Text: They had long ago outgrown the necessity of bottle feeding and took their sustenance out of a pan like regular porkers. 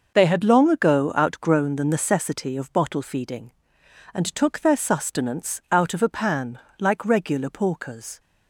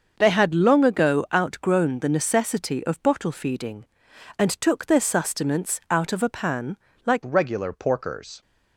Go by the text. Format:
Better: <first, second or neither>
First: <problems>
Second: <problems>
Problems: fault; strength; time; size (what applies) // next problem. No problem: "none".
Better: first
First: pauses between "pan" and "like"; slight; at 6.5 s; 0.22 s long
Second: starts louder than the rest; until 1.1 s; 6.5 dB // pauses between "pan" and "like"; slight; at 6.7 s; 0.30 s long // changes voice at "regular"; from 7.2 s on; 1.2 s long